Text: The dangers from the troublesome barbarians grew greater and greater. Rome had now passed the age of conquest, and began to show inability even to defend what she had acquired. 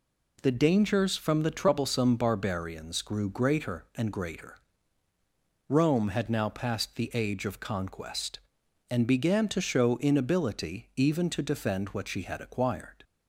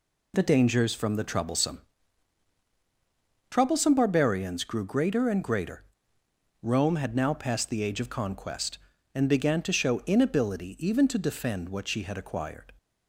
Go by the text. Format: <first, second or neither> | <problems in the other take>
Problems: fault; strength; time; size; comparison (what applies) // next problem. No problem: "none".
first | says "troublesome" twice; at 3.5 s